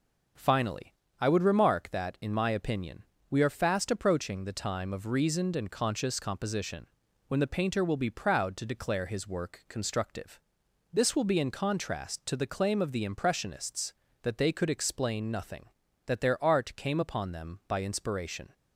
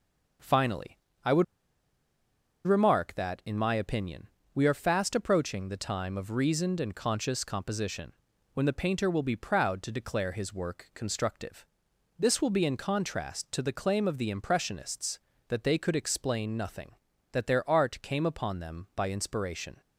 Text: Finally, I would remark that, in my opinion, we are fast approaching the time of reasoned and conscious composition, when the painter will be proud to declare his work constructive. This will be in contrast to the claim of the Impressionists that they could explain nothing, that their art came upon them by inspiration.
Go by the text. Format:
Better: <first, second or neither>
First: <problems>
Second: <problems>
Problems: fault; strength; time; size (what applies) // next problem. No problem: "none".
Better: first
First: none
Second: pauses between "would" and "remark"; at 1.4 s; 1.2 s long